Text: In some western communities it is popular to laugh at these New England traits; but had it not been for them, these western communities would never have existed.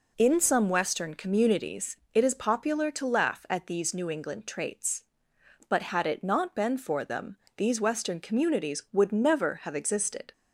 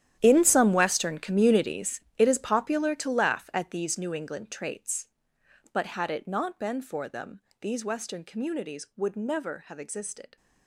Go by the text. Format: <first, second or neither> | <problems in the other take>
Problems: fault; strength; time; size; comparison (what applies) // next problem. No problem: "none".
first | gets quieter; strong; throughout; 15.5 dB // pauses between "communities" and "it"; slight; at 1.9 s; 0.18 s long; slight in the first